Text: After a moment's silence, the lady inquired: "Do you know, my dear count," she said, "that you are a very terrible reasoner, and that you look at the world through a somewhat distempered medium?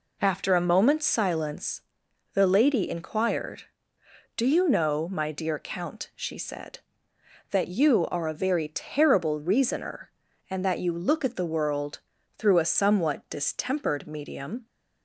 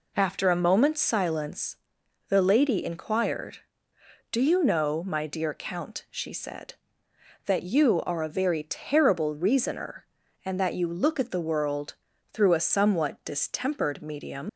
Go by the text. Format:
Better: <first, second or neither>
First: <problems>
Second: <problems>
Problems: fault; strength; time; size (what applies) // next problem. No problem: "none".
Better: first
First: pauses between "world" and "through"; at 11.9 s; 0.40 s long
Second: pauses between "world" and "through"; at 11.9 s; 0.40 s long // leaves "medium" unfinished; at 14.4 s; 105 ms